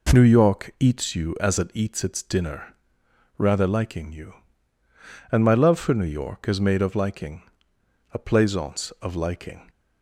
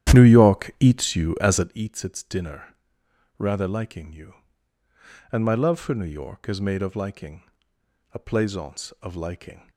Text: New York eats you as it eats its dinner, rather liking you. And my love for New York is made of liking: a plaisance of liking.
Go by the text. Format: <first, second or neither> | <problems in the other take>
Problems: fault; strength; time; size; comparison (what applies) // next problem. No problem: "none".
first | starts louder than the rest; strong; until 1.7 s; 11 dB